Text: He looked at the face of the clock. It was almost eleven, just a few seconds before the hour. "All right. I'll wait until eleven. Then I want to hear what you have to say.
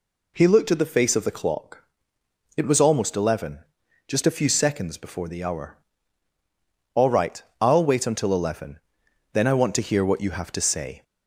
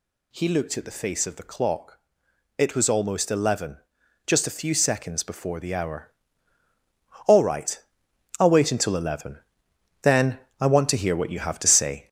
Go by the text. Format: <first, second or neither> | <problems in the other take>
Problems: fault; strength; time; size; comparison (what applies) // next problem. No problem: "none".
first | gets louder; noticeable; throughout; 5 dB // pauses between "Then" and "I"; slight; at 10.3 s; 0.20 s long